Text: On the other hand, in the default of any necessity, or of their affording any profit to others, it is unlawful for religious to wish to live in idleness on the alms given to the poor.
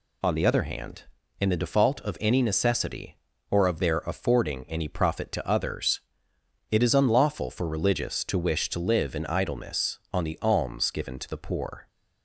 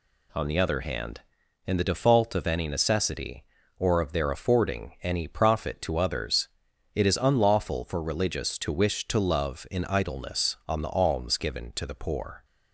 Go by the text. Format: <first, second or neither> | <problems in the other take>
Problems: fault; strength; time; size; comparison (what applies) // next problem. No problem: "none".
first | says "love" for "live"; at 9.1 s